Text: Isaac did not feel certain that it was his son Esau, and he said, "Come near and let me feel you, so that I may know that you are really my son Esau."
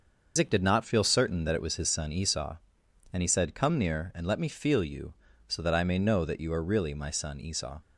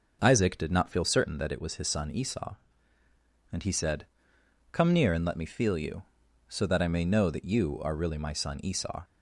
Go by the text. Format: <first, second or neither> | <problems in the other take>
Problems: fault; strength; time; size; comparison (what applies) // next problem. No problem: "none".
second | loses the start of "Isaac"; at 0.3 s; 130 ms // starts louder than the rest; until 1.3 s; 6 dB; noticeable in the second